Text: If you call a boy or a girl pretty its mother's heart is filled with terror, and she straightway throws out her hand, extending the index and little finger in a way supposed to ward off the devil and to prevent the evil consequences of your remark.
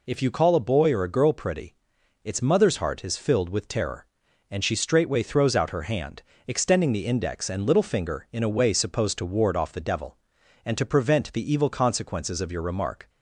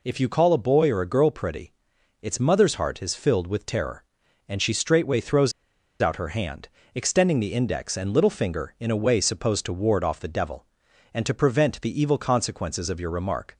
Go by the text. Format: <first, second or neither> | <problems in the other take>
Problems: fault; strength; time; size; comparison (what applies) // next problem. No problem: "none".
first | pauses between "pretty" and "its"; noticeable; at 1.7 s; 0.48 s long; noticeable in the first // pauses between "throws" and "out"; noticeable; at 5.5 s; 0.49 s long